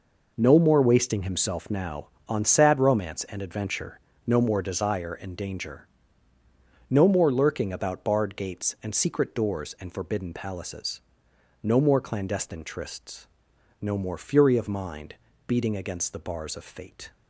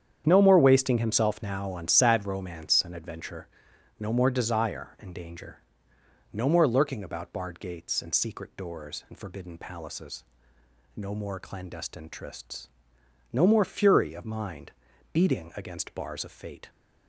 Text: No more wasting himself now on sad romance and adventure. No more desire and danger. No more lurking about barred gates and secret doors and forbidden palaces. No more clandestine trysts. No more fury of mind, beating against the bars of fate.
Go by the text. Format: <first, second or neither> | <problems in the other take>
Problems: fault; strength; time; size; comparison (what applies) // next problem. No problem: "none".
first | starts louder than the rest; strong; until 1.2 s; 8.5 dB // skips "the"; at 15.9 s